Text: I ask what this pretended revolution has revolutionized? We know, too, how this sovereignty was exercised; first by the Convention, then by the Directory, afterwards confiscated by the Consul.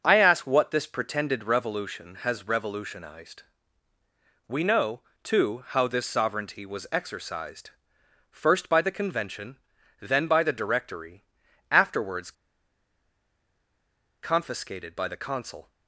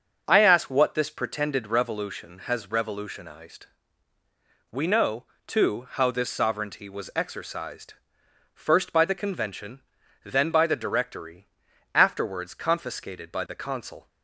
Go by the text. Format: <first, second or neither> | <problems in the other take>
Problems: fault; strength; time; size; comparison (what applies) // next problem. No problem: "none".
second | starts louder than the rest; until 1.0 s; 6 dB; also in the second // pauses between "afterwards" and "confiscated"; strong; at 12.3 s; 1.9 s long